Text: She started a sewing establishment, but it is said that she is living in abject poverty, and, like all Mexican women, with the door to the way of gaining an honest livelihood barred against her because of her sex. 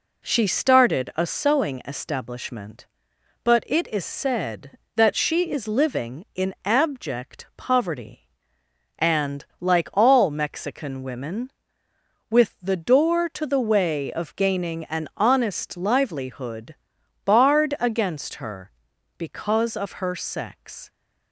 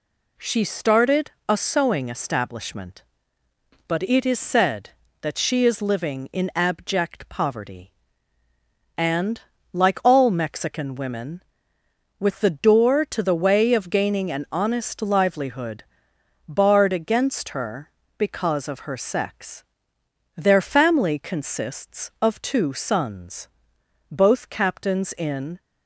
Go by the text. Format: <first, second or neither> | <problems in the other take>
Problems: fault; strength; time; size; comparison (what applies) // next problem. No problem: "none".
first | pauses between "started" and "a"; slight; at 1.2 s; 0.18 s long // pauses between "livelihood" and "barred"; noticeable; at 15.8 s; 0.64 s long; noticeable in the first // goes on to say "Their family consists of two sons both captains in"; strong; from 20.3 s on; 5.2 s long